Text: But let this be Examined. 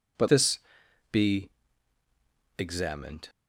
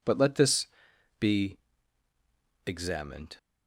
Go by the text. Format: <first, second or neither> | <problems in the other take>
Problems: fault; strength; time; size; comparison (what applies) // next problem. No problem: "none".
second | skips "let"; at 0.2 s // pauses between "this" and "be"; noticeable; at 0.5 s; 0.52 s long; noticeable in the second // pauses between "be" and "Examined"; at 1.4 s; 1.0 s long; also in the second